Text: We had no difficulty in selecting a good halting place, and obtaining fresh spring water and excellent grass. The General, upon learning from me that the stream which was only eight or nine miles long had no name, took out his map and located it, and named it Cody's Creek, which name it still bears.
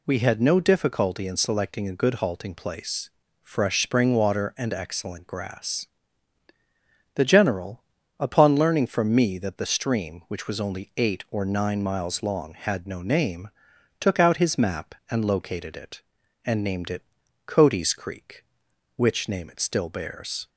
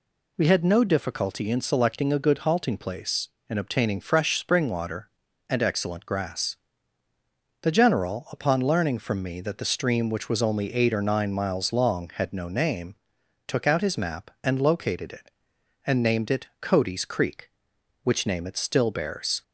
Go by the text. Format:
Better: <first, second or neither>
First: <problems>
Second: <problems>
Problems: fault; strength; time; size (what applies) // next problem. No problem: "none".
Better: second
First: skips "and obtaining"; at 3.2 s // pauses between "it" and "Cody's"; noticeable; at 17.0 s; 0.46 s long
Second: none